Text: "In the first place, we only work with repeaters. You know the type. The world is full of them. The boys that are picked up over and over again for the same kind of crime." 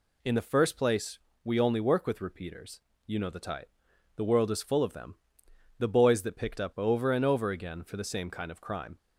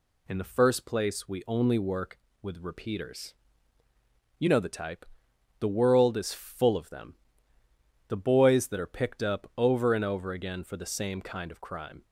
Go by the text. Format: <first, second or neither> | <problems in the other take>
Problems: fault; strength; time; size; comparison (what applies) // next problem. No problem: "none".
second | skips "are"; at 6.3 s